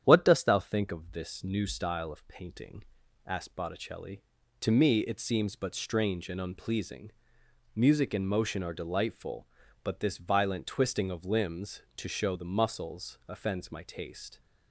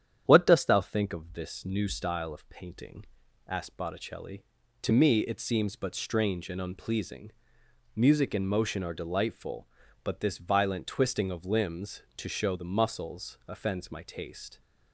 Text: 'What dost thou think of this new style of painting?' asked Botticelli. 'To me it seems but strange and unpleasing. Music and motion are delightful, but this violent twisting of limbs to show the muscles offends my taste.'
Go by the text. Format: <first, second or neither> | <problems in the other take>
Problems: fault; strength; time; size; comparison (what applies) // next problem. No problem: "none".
neither | starts louder than the rest; strong; the same in both